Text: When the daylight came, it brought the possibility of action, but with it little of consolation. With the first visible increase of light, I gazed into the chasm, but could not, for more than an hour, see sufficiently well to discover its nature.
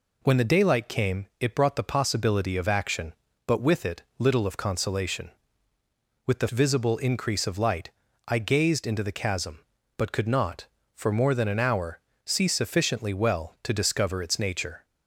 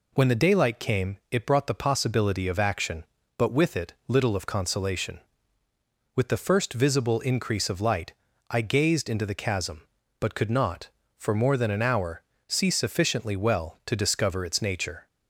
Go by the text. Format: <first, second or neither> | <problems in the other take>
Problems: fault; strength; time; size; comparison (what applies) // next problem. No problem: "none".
second | pauses between "it" and "little"; slight; at 4.0 s; 0.16 s long // skips "first"; at 6.4 s